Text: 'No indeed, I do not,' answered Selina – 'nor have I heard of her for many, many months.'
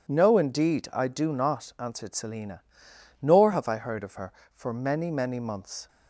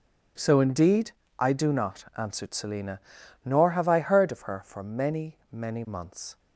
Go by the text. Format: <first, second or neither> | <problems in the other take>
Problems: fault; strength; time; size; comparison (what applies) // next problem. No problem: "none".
first | says "So" for "No"; at 0.3 s